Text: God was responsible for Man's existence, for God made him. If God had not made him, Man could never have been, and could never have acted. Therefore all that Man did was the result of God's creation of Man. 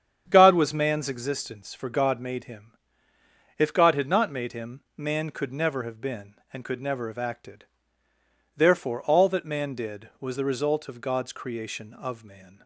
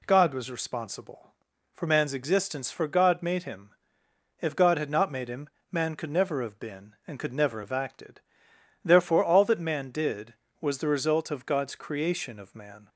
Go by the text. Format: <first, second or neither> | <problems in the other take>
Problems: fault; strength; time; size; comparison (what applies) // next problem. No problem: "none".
second | starts louder than the rest; strong; until 1.2 s; 8 dB // skips "responsible for"; at 0.7 s